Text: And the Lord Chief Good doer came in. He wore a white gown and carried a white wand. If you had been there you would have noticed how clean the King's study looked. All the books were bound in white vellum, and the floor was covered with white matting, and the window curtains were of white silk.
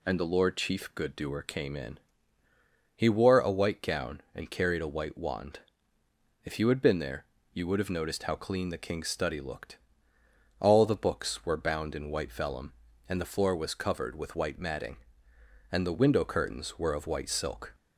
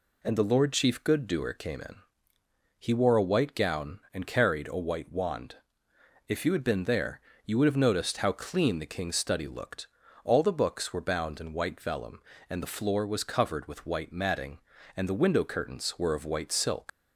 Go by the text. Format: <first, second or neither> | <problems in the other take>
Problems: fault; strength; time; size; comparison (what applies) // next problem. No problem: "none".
first | pauses between "there" and "you"; slight; at 7.1 s; 0.26 s long; slight in the first // leaves "silk" unfinished; at 16.8 s; 150 ms